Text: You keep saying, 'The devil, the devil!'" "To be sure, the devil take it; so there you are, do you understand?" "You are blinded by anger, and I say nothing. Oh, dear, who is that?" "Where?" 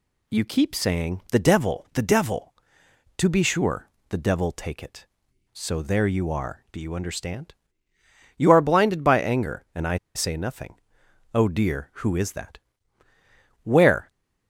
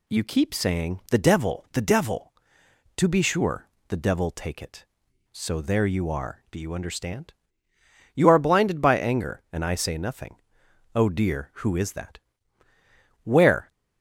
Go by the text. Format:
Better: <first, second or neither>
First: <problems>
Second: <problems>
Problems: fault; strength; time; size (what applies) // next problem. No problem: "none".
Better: second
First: pauses between "I" and "say"; slight; at 9.9 s; 0.19 s long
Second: none